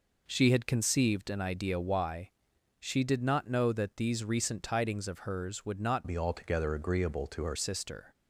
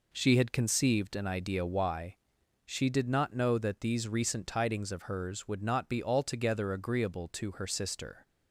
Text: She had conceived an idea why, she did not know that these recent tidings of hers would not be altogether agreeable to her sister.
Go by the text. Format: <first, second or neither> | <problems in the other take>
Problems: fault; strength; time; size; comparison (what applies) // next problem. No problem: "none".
second | changes voice from "be" to "her"; from 6.0 to 7.5 s; 1.5 s long